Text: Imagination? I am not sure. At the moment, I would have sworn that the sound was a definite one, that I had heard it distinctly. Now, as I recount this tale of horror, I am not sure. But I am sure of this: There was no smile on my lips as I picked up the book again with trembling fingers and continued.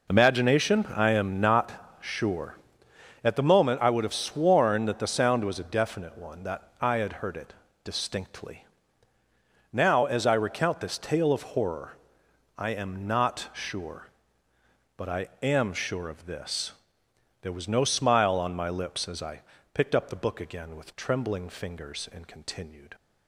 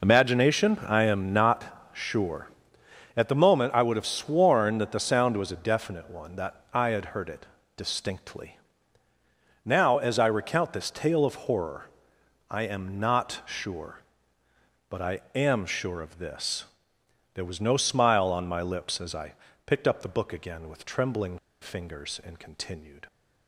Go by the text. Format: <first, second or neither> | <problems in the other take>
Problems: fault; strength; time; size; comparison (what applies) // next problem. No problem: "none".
first | pauses between "it" and "distinctly"; slight; at 7.4 s; 0.32 s long; slight in the first // pauses between "I" and "picked"; slight; at 19.3 s; 0.32 s long; slight in the first // pauses between "trembling" and "fingers"; slight; at 21.3 s; 0.23 s long